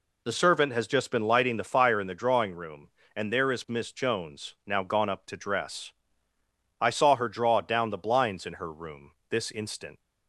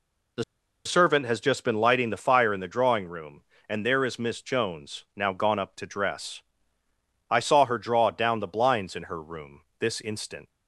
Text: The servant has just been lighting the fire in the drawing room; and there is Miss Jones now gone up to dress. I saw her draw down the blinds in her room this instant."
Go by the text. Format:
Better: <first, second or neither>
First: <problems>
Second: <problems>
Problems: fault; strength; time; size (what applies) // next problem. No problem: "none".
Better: first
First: pauses between "room" and "this"; slight; at 9.1 s; 0.16 s long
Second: pauses between "The" and "servant"; at 0.4 s; 0.42 s long // pauses between "room" and "this"; slight; at 9.6 s; 0.16 s long